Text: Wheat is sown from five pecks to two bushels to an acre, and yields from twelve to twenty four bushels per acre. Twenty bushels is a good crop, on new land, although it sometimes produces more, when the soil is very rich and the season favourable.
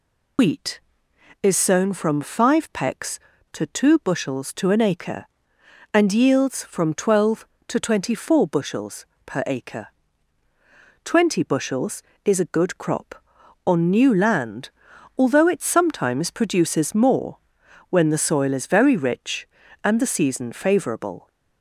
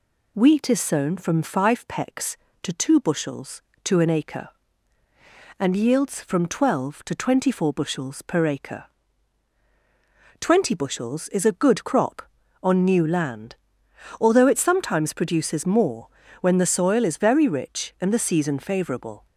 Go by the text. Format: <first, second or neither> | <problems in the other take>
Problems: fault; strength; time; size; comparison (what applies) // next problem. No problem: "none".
second | loses the start of "Wheat"; at 0.3 s; 100 ms // pauses between "bushels" and "per"; slight; at 9.0 s; 0.22 s long